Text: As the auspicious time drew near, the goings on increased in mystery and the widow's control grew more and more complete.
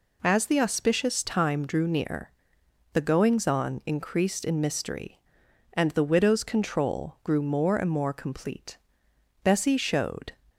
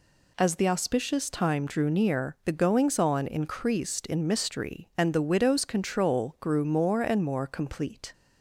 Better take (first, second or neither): second